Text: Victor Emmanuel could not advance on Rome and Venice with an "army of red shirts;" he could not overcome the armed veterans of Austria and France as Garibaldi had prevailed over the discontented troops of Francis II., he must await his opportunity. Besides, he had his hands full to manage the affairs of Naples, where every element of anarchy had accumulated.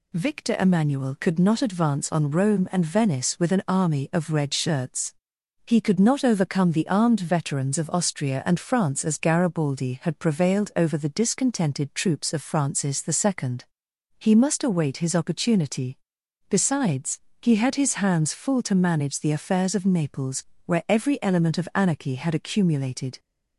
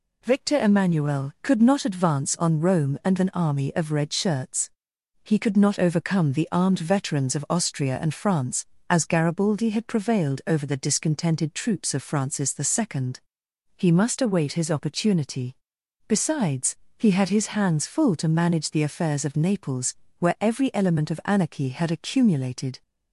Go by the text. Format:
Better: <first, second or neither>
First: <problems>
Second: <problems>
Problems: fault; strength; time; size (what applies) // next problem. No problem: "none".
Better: first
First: none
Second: skips "Venice with"; at 3.1 s